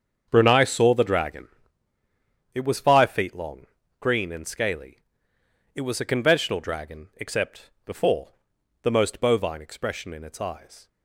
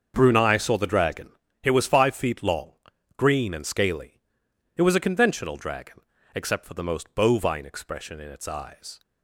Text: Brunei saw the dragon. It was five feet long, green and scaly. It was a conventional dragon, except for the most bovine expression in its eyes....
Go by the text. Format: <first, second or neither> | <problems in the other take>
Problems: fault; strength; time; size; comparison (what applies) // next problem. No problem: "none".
second | starts louder than the rest; strong; until 1.3 s; 7.5 dB; also in the second // says "before" for "for"; at 7.8 s